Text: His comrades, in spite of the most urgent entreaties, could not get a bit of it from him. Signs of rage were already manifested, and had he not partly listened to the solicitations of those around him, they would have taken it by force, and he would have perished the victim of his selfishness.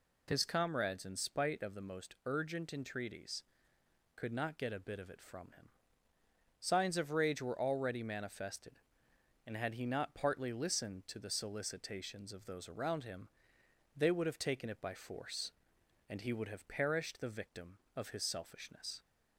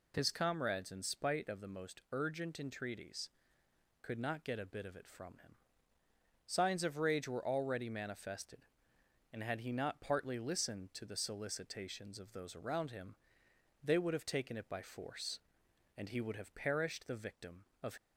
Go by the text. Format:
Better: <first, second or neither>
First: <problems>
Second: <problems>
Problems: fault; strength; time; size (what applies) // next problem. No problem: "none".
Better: first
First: none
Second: stops before "his selfishness"; at 17.9 s